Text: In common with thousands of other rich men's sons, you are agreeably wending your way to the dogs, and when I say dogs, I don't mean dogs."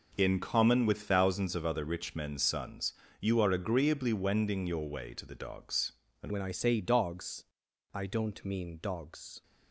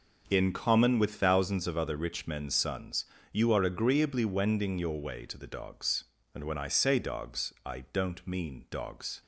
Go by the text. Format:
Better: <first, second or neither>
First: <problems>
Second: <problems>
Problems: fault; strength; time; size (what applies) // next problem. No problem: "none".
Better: second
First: changes voice at "when"; from 6.3 s on; 3.1 s long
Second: none